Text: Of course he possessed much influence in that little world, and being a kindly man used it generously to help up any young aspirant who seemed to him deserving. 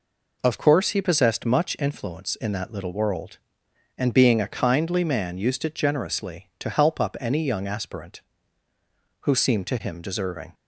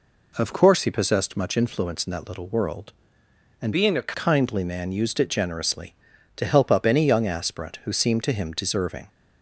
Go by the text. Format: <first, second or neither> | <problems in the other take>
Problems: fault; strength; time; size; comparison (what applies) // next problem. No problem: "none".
first | changes voice from "being" to "a"; from 3.7 to 4.1 s; 0.4 s long